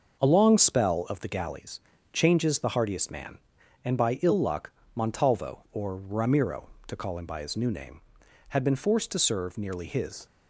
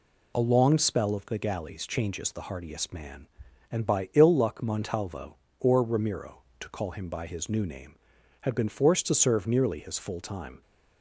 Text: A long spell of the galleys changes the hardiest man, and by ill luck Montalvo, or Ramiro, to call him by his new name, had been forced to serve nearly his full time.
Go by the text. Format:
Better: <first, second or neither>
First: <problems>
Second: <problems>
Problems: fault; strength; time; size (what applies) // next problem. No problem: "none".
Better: second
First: starts louder than the rest; noticeable; until 1.2 s; 6 dB // pauses between "galleys" and "changes"; slight; at 1.7 s; 0.32 s long // pauses between "luck" and "Montalvo"; slight; at 4.7 s; 0.24 s long // stops before "full time"; at 10.2 s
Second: none